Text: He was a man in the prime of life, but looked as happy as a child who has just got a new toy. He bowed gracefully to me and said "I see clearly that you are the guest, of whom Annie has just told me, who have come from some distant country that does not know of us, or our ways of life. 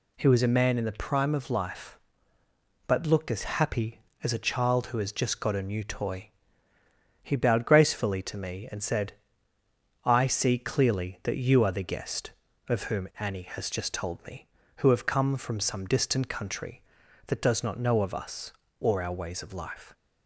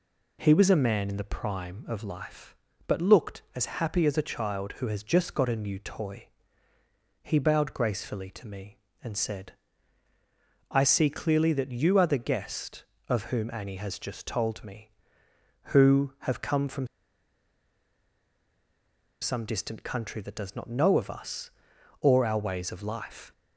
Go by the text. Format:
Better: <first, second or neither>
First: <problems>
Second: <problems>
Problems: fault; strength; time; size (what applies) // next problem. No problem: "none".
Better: first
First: pauses between "said" and "I"; noticeable; at 9.1 s; 0.90 s long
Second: pauses between "said" and "I"; at 9.5 s; 1.1 s long // pauses between "from" and "some"; strong; at 16.8 s; 2.3 s long